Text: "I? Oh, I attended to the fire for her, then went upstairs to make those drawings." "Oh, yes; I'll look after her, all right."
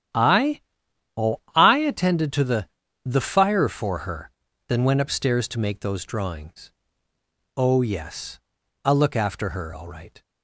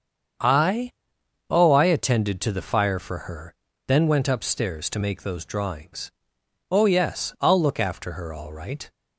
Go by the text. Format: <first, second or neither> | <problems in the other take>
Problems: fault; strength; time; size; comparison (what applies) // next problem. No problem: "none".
second | starts louder than the rest; strong; until 1.8 s; 10 dB; strong in the second // says "the" twice; at 3.0 s